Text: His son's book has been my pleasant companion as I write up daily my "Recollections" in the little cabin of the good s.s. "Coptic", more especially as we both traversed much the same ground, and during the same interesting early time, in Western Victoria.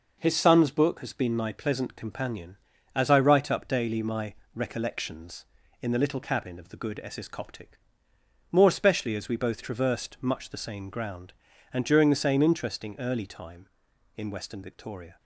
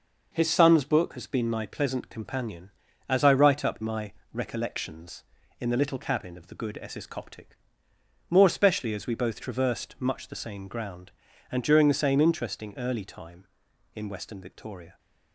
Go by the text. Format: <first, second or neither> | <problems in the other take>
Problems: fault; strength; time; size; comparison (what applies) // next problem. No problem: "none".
first | skips "daily"; at 3.8 s // pauses between "my" and "Recollections"; slight; at 4.1 s; 0.18 s long; slight in the first